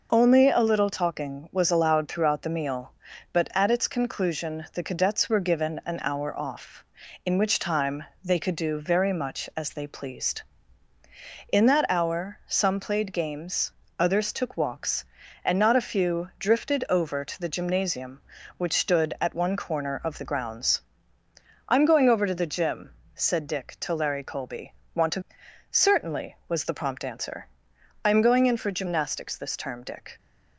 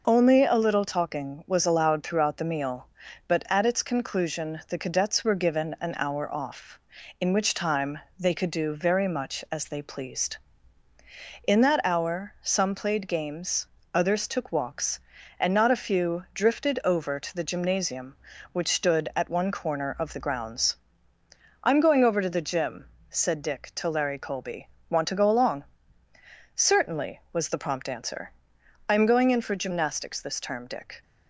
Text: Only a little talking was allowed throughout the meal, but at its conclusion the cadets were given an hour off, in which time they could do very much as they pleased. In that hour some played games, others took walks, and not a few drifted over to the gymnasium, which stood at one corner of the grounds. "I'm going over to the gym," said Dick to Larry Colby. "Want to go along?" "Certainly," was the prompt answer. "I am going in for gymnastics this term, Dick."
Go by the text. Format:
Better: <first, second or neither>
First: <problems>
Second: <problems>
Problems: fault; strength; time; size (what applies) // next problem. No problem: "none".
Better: second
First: pauses between "time" and "they"; slight; at 8.0 s; 0.18 s long // skips "go along"; at 25.4 s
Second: pauses between "time" and "they"; slight; at 7.9 s; 0.18 s long